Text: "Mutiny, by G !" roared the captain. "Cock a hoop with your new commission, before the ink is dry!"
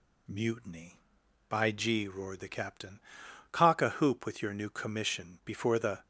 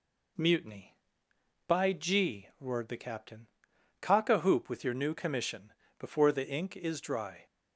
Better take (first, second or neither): second